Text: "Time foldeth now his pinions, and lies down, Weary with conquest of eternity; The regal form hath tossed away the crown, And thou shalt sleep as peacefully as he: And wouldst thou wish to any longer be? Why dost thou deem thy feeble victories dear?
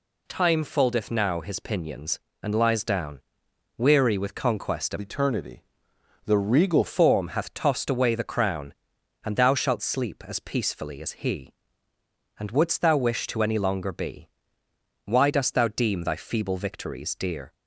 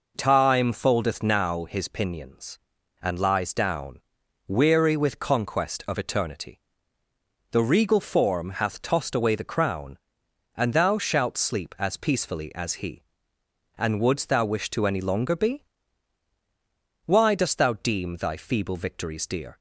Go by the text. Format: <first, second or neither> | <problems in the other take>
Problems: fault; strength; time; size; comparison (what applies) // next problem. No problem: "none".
second | changes voice from "eternity" to "regal"; from 5.0 to 6.8 s; 1.8 s long